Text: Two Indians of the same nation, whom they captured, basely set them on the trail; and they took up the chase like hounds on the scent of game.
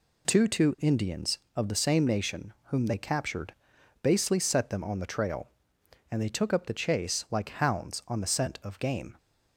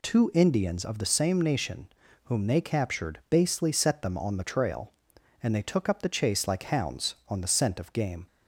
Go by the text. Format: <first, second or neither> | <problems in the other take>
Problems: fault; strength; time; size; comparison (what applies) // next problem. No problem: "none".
second | says "Two" twice; at 0.4 s